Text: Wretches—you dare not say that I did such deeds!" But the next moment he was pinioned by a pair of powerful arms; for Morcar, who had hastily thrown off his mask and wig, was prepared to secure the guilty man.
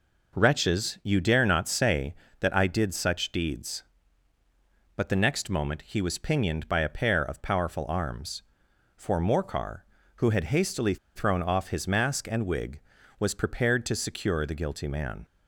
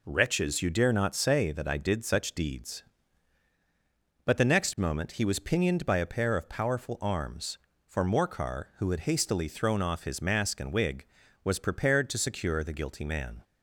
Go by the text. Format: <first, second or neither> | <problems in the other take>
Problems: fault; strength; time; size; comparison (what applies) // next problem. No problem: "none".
second | pauses between "hastily" and "thrown"; slight; at 10.9 s; 0.19 s long